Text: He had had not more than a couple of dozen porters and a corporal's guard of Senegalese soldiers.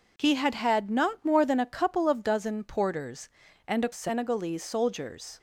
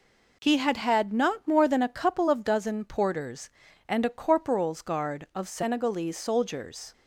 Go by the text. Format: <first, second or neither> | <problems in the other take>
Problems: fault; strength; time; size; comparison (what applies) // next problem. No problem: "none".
second | skips "corporal's guard of"; at 3.9 s